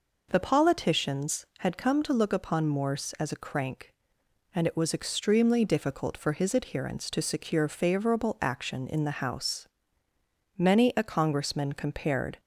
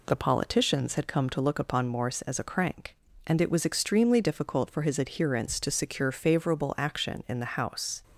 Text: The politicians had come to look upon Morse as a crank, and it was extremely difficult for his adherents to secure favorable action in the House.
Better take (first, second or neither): second